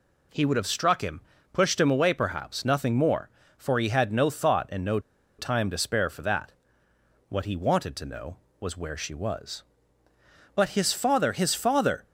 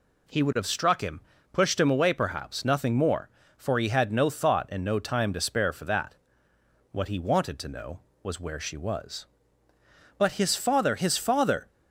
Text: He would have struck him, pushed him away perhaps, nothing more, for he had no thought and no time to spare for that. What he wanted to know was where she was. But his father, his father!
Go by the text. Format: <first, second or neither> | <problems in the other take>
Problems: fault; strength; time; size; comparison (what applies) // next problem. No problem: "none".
second | pauses between "no" and "time"; at 4.9 s; 0.39 s long